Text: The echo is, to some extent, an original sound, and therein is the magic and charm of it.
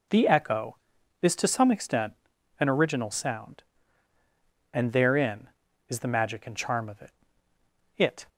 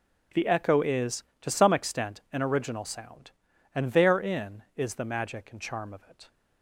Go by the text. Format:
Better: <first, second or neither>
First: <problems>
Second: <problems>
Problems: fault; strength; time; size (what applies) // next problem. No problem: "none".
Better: second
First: says "it" twice; at 7.9 s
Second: none